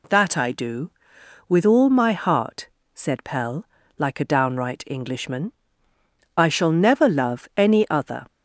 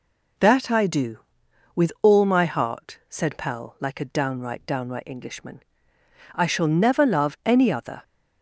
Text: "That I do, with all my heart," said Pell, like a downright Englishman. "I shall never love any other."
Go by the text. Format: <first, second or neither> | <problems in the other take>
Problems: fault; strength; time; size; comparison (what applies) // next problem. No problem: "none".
first | says "downright" twice; at 4.6 s